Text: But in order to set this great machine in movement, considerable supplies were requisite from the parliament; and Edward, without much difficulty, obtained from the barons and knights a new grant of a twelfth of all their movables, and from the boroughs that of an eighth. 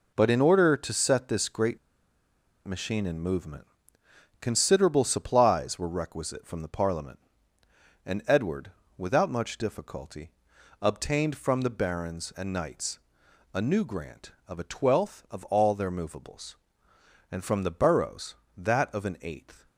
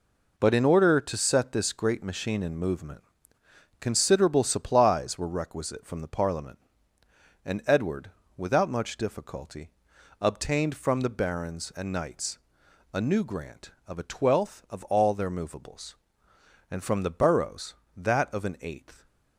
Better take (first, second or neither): second